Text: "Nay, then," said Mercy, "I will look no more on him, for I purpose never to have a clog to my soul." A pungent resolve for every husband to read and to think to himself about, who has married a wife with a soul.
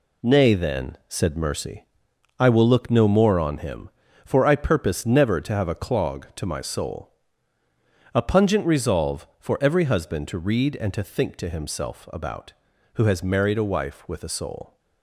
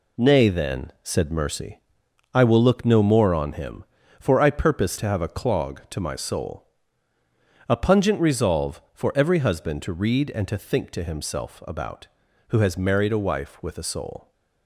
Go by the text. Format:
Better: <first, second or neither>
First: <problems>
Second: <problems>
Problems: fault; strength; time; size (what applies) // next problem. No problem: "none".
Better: first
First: none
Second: skips "never"; at 4.9 s